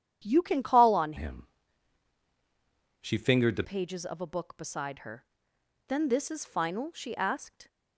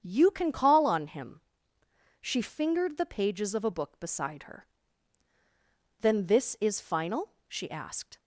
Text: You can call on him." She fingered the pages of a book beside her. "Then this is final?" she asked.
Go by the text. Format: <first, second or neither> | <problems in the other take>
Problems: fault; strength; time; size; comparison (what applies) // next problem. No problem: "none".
second | starts louder than the rest; strong; until 1.2 s; 9.5 dB; strong in the second // changes voice from "him" to "the"; from 1.1 to 3.6 s; 2.5 s long